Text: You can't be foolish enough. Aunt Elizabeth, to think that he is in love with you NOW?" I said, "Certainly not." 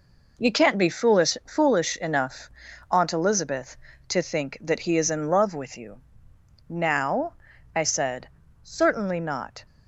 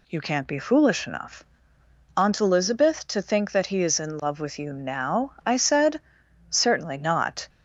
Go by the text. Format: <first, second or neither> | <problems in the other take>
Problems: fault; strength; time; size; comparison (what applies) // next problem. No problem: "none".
second | says "foolish" twice; at 1.4 s // pauses between "you" and "NOW"; noticeable; at 5.9 s; 0.70 s long